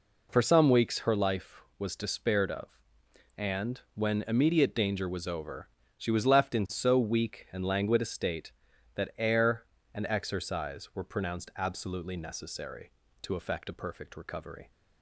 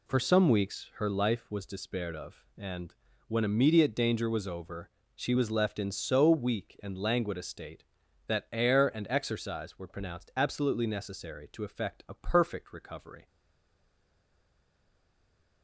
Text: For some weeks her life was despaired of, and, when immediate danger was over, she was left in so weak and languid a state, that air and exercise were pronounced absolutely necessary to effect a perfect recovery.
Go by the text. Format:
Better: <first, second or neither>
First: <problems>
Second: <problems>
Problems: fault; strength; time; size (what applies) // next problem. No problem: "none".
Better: first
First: none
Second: stays silent after the last word; from 13.2 s on; 2.4 s long